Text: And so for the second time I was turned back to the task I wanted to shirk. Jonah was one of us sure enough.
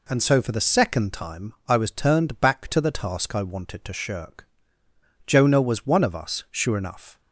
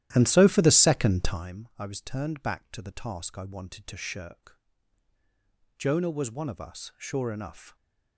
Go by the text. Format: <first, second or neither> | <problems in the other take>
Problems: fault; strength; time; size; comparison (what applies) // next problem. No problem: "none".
first | starts louder than the rest; strong; until 1.5 s; 13 dB